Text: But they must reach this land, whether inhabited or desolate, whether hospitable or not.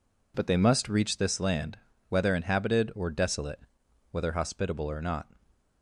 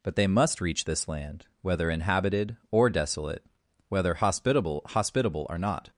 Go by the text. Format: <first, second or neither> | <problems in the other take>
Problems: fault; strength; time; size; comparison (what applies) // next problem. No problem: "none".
first | says "hospitable" twice; at 4.8 s